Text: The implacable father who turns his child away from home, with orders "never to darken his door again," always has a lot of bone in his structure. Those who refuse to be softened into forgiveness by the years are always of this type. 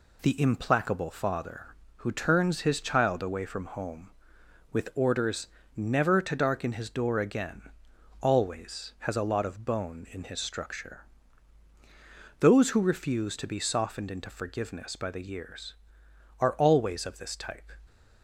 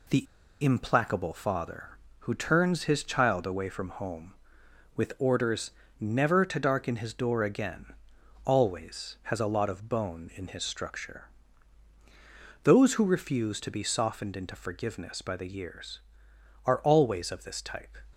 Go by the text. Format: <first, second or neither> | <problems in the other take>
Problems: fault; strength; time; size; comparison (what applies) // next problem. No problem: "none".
first | pauses between "The" and "implacable"; at 0.2 s; 0.38 s long // pauses between "orders" and "never"; slight; at 5.7 s; 0.30 s long; slight in the first